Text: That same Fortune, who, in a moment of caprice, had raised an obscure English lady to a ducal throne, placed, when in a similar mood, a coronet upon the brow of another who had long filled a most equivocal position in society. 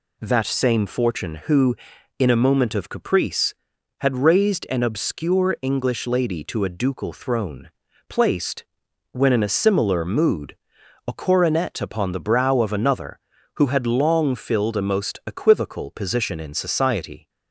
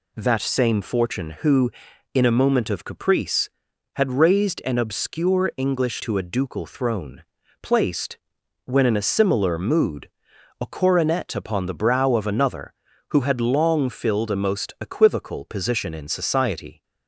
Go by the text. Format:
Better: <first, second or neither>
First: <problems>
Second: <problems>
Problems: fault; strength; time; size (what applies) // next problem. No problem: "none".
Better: first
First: none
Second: skips "lady"; at 6.0 s